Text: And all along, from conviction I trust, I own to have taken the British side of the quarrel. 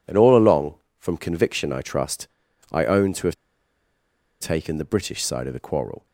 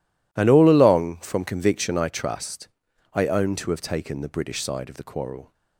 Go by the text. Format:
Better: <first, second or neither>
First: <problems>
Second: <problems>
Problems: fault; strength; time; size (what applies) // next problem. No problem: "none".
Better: second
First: pauses between "have" and "taken"; at 3.3 s; 1.0 s long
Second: none